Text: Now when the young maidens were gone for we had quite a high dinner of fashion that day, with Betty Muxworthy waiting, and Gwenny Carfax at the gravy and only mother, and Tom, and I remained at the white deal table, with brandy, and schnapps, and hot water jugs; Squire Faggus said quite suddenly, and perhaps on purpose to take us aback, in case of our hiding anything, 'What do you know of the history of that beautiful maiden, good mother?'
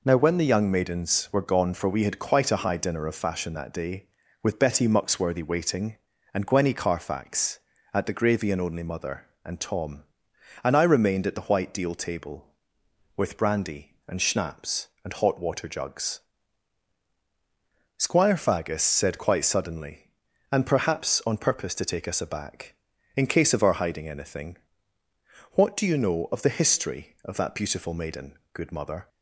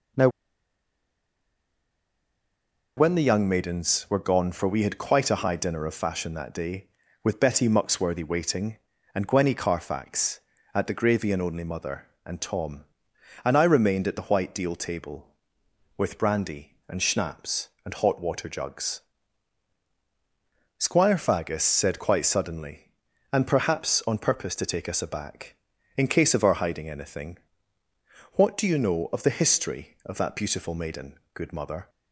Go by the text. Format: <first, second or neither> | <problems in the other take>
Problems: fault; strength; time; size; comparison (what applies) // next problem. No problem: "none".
first | pauses between "Now" and "when"; strong; at 0.2 s; 2.6 s long